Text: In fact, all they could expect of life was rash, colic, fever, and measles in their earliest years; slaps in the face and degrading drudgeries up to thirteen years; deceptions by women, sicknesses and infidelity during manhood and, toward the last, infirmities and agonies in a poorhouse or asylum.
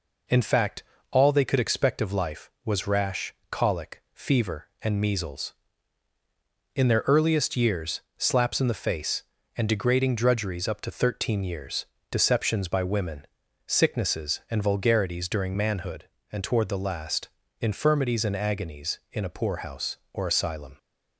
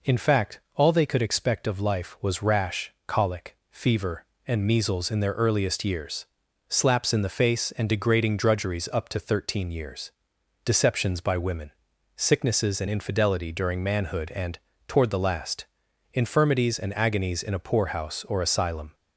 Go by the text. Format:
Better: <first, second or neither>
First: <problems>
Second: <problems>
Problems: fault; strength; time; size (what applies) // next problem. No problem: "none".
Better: second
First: says "vulgarities" for "infidelity"; at 14.6 s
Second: none